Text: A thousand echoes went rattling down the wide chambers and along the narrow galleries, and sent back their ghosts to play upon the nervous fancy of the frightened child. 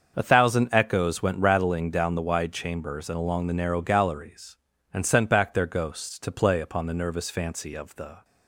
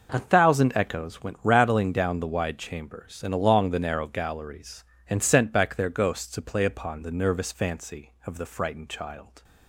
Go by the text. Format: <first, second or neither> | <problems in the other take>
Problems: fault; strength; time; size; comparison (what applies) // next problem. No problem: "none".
second | starts louder than the rest; until 1.1 s; 6.5 dB // stops before "frightened child"; at 8.2 s